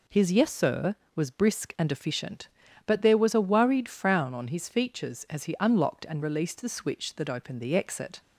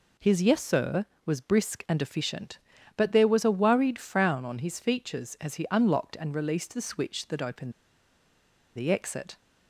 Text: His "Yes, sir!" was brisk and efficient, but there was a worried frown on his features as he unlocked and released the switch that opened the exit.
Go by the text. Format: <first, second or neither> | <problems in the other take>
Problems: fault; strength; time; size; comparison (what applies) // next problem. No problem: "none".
first | pauses between "opened" and "the"; at 7.7 s; 1.0 s long